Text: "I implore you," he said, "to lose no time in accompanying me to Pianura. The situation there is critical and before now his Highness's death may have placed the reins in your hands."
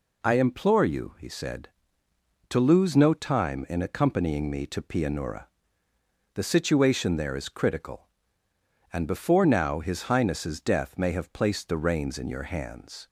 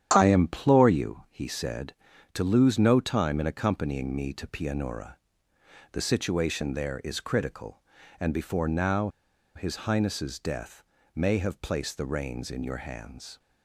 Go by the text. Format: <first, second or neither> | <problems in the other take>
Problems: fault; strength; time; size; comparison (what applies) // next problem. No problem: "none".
first | starts louder than the rest; strong; until 1.1 s; 9.5 dB // pauses between "now" and "his"; noticeable; at 9.0 s; 0.47 s long // pauses between "death" and "may"; slight; at 10.8 s; 0.32 s long